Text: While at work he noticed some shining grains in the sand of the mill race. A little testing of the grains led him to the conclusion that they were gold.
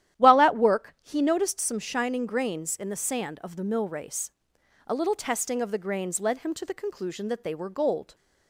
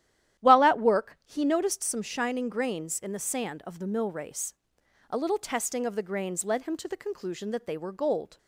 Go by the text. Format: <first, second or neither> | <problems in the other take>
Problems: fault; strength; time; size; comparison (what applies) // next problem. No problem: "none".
neither | starts louder than the rest; strong; the same in both